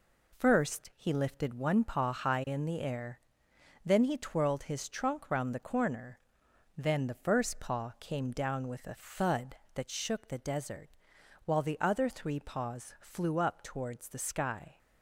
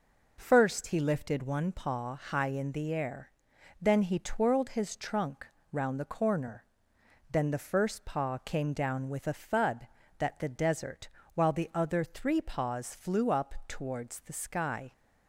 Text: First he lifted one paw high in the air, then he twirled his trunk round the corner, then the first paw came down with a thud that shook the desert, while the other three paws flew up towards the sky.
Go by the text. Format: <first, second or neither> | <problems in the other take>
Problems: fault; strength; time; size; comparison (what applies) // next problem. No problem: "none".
first | pauses between "trunk" and "round"; slight; at 5.4 s; 0.26 s long // skips "shook"; at 10.3 s